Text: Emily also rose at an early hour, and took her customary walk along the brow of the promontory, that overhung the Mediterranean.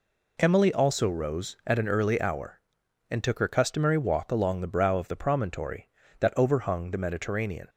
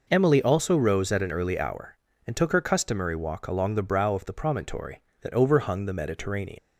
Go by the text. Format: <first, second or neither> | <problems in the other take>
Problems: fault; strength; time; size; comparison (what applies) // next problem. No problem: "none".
first | leaves "Mediterranean" unfinished; at 6.5 s; 85 ms